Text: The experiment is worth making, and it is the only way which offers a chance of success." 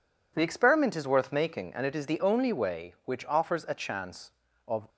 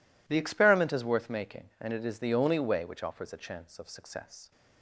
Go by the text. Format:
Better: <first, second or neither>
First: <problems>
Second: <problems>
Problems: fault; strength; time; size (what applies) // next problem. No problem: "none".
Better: second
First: stops before "success"; at 4.8 s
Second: none